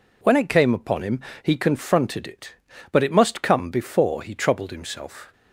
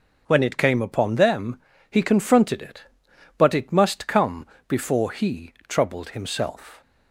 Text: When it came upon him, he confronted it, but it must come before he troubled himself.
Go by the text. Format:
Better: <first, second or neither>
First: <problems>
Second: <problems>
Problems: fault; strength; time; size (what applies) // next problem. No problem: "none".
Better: first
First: none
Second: says "them" for "him"; at 1.1 s // pauses between "come" and "before"; slight; at 4.4 s; 0.20 s long